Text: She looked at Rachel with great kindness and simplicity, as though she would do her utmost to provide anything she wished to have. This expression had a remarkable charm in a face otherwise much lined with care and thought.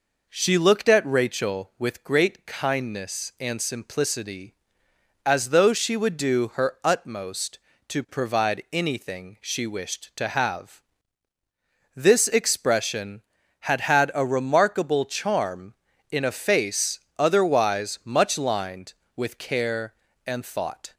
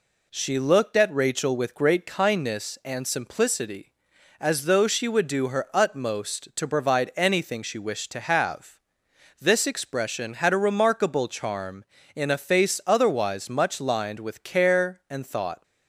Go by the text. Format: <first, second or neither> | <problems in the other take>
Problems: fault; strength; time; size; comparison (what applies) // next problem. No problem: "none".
second | says "had" twice; at 13.8 s // pauses between "face" and "otherwise"; slight; at 16.9 s; 0.18 s long